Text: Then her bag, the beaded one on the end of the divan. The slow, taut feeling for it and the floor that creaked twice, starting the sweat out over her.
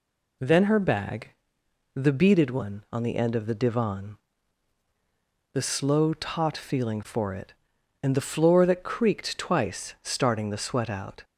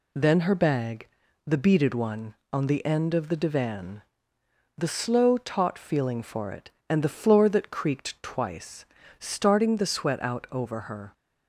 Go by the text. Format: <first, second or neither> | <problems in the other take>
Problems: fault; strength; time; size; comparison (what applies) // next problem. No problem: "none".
second | stops before "over her"; at 11.2 s